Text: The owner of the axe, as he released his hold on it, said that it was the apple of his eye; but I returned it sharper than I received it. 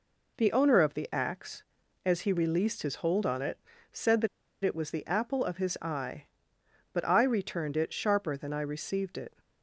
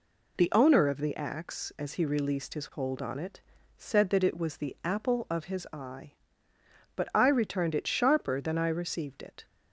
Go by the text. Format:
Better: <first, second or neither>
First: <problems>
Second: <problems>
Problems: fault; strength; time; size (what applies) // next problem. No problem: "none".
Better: second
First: pauses between "that" and "it"; at 4.2 s; 0.37 s long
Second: none